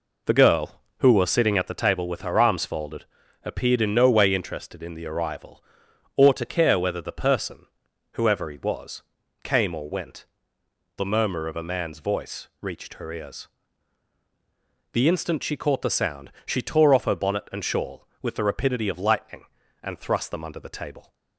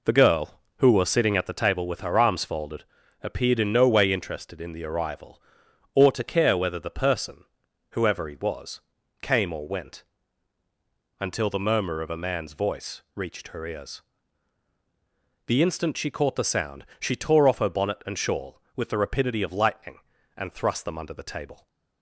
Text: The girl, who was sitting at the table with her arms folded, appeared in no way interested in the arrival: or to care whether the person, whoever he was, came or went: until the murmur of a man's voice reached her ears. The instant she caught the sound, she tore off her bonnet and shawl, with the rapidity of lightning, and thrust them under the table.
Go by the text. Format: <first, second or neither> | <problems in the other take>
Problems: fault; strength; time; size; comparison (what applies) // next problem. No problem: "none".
second | skips "until"; at 10.6 s